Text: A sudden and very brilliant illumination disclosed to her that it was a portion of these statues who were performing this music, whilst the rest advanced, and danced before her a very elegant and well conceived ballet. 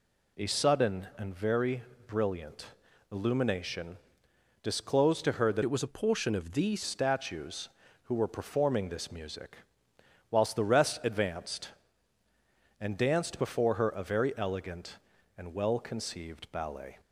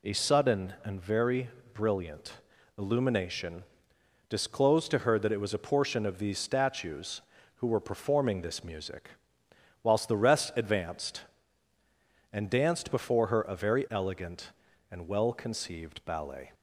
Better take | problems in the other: second | pauses between "very" and "brilliant"; slight; at 1.8 s; 0.24 s long; slight in the second // pauses between "brilliant" and "illumination"; at 2.6 s; 0.44 s long; also in the second // pauses between "illumination" and "disclosed"; noticeable; at 3.9 s; 0.66 s long; noticeable in the second // changes voice from "it" to "these"; from 5.6 to 6.8 s; 1.2 s long

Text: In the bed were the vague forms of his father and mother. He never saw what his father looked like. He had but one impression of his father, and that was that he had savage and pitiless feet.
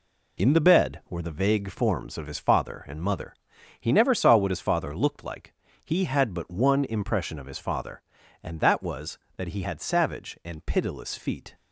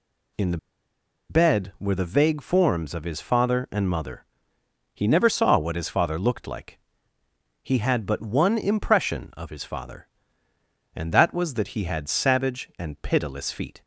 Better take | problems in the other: first | pauses between "the" and "bed"; noticeable; at 0.5 s; 0.72 s long

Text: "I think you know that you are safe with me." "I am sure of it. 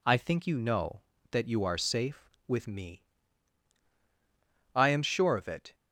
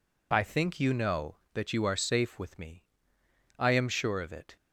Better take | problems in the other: neither | none

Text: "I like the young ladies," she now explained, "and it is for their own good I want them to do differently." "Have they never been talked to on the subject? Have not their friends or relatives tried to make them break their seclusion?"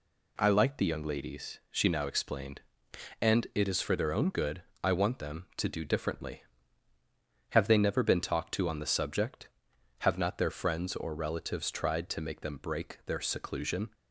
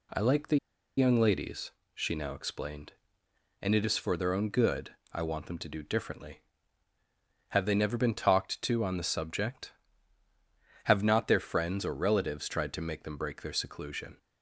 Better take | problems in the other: first | pauses between "the" and "young"; at 0.5 s; 0.40 s long // pauses between "good" and "I"; slight; at 4.9 s; 0.16 s long; slight in the first

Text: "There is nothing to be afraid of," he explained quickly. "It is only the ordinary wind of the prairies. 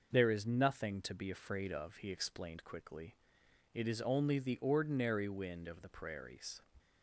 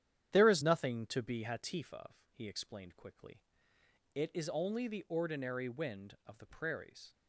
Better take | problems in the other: first | starts louder than the rest; strong; until 1.3 s; 10.5 dB // says "hatif" for "afraid"; at 1.4 s

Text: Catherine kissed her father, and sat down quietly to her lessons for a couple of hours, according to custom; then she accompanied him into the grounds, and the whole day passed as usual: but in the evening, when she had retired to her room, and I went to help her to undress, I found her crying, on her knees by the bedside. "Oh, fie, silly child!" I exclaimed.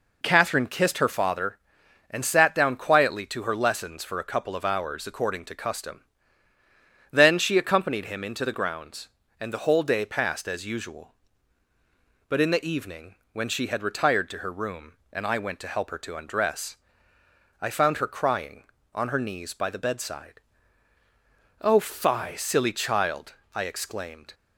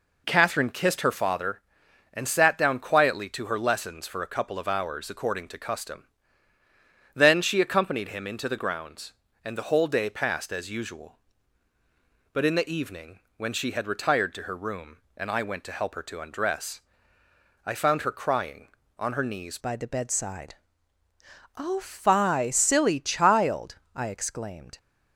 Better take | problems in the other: first | changes voice at "by"; from 19.5 s on; 5.2 s long

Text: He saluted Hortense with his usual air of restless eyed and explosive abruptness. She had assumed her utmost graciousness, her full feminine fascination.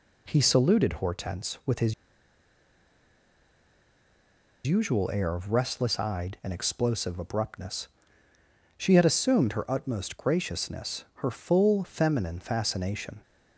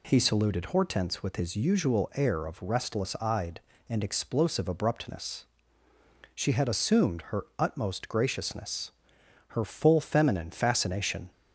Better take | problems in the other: second | pauses between "his" and "usual"; strong; at 1.9 s; 2.7 s long

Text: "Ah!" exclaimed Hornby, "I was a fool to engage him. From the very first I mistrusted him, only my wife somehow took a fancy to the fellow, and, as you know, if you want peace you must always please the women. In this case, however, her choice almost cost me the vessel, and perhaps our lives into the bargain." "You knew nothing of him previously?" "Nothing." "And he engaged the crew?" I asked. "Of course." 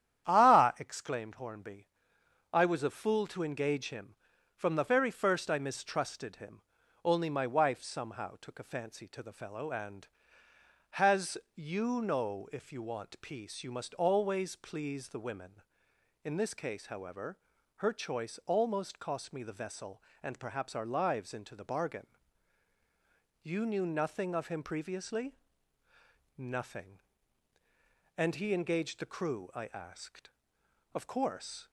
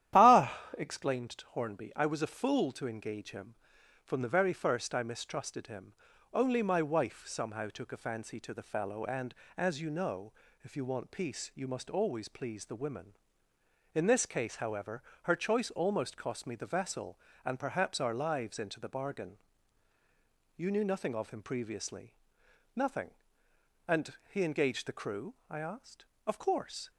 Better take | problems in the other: second | starts louder than the rest; strong; until 1.3 s; 10 dB; strong in the second // says "has" for "as"; at 10.9 s

